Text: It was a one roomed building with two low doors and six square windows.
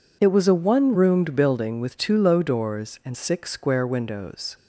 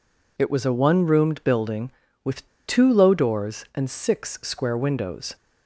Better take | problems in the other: first | pauses between "with" and "two"; slight; at 2.4 s; 0.20 s long

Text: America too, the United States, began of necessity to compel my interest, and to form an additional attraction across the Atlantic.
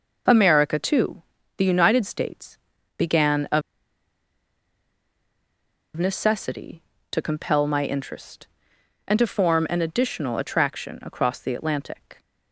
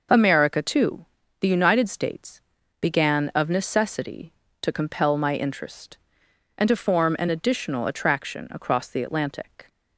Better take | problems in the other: second | pauses between "of" and "necessity"; strong; at 3.6 s; 2.3 s long

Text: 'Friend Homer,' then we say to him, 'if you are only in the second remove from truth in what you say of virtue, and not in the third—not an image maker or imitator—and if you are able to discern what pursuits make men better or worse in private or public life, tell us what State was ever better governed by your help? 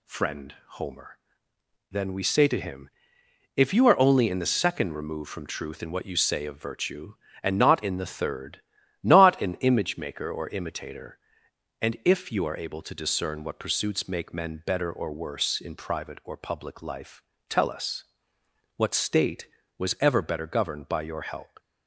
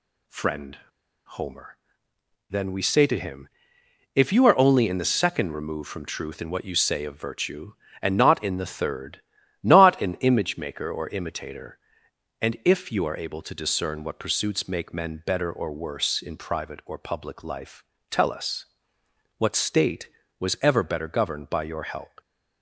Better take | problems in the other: first | pauses between "Friend" and "Homer"; noticeable; at 0.7 s; 0.49 s long // pauses between "us" and "what"; noticeable; at 18.6 s; 0.74 s long; noticeable in the first

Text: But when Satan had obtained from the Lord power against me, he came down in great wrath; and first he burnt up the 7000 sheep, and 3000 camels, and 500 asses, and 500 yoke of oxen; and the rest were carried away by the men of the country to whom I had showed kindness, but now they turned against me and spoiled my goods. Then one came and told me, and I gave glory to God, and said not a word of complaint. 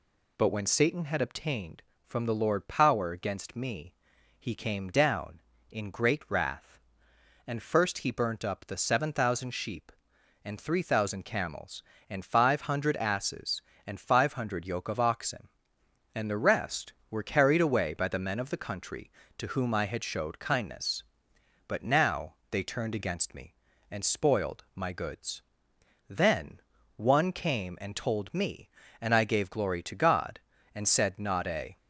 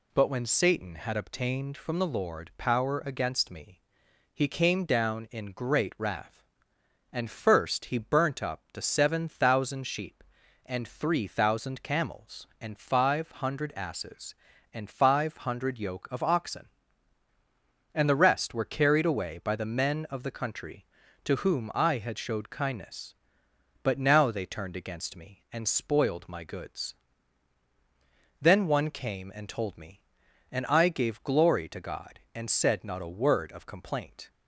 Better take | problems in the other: second | pauses between "now" and "they"; slight; at 22.3 s; 0.16 s long // pauses between "Then" and "one"; at 26.5 s; 0.38 s long // stops before "word of complaint"; at 31.7 s

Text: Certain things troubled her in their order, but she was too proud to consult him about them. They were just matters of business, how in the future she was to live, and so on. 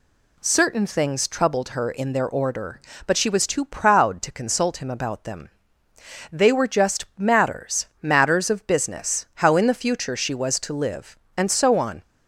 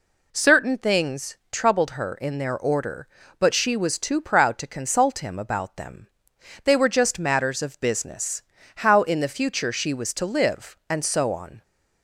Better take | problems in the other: second | says "matters" twice; at 8.0 s

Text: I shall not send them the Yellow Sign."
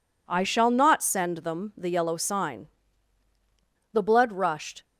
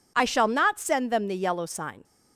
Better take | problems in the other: second | goes on to say "The blood rushed"; noticeable; from 3.9 s on; 0.92 s long

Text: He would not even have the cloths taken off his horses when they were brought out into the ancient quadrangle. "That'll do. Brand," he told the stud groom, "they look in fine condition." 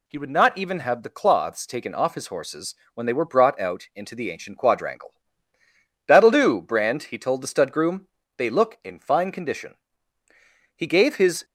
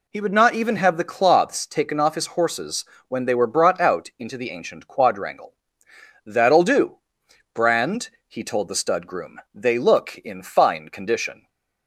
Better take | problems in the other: second | pauses between "horses" and "when"; slight; at 2.7 s; 0.20 s long; slight in the second // goes on to say "He gave his"; noticeable; from 10.7 s on; 0.68 s long

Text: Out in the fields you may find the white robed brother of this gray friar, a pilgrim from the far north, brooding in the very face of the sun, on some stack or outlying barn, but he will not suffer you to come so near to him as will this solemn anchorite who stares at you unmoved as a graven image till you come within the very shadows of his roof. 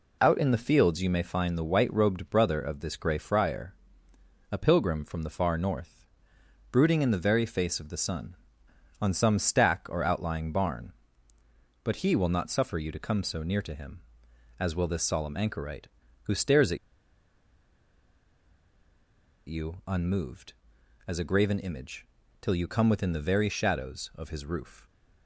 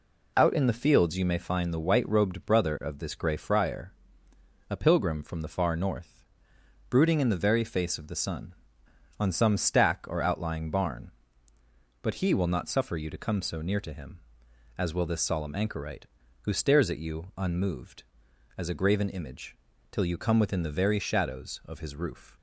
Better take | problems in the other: second | pauses between "at" and "you"; strong; at 16.7 s; 2.7 s long // pauses between "image" and "till"; slight; at 22.0 s; 0.34 s long; slight in the second

